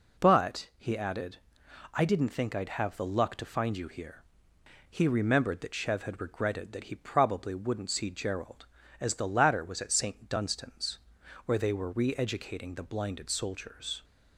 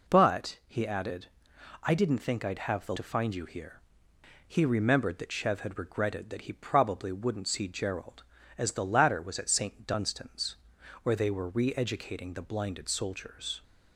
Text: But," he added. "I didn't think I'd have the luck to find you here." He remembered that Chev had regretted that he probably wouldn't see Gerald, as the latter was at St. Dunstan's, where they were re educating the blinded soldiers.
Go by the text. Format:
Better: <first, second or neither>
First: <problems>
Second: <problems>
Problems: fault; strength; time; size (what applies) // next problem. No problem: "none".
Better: first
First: none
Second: skips "luck"; at 2.9 s